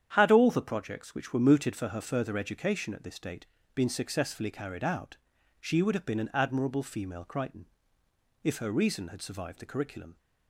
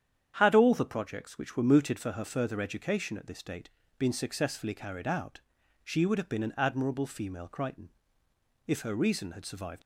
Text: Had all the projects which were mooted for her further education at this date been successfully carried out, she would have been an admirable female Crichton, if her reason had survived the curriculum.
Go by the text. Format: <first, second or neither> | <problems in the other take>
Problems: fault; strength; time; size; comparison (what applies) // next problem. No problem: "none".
first | starts louder than the rest; strong; until 1.3 s; 9 dB; strong in the first // pauses between "date" and "been"; slight; at 3.6 s; 0.30 s long; slight in the first // stops before "the curriculum"; at 9.8 s